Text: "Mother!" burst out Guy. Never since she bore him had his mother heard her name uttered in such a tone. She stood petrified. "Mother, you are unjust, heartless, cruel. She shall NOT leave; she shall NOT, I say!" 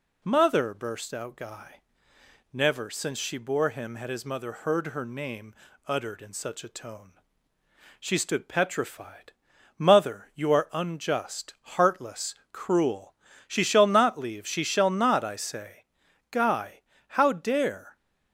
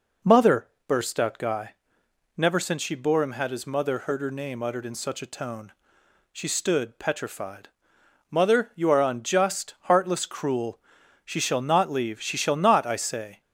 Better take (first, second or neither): second